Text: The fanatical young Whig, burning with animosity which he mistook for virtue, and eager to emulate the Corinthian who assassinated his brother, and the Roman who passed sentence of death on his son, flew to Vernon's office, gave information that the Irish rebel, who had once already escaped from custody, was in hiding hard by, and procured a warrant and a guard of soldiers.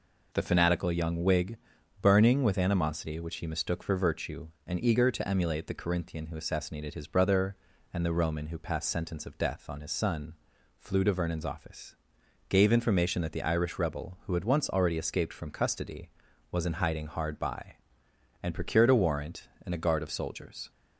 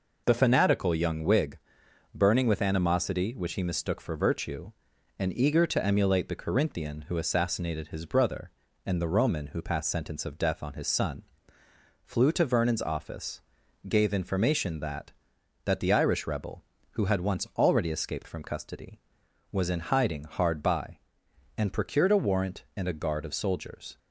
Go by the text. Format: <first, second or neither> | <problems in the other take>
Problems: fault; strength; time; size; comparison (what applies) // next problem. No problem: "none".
first | says "that" twice; at 15.6 s